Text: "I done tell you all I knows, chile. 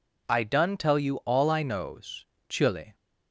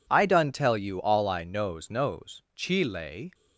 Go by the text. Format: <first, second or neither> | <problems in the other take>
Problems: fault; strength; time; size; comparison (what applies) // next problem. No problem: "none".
first | says "knows" twice; at 1.8 s